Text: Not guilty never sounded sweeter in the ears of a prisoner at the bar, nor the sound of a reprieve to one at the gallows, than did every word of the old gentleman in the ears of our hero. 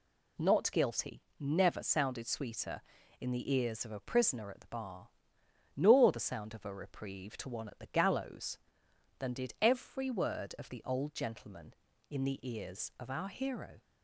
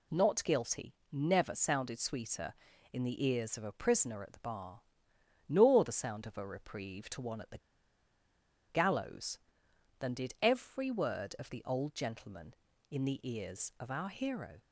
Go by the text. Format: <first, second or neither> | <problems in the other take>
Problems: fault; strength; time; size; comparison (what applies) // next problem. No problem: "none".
first | pauses between "guilty" and "never"; slight; at 0.9 s; 0.16 s long; slight in the first // pauses between "the" and "gallows"; at 7.5 s; 1.0 s long